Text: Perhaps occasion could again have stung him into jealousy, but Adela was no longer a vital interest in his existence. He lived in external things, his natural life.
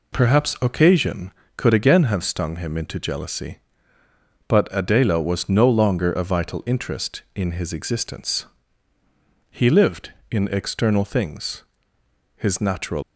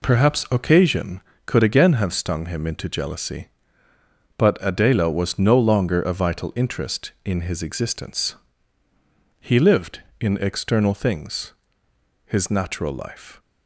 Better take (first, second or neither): second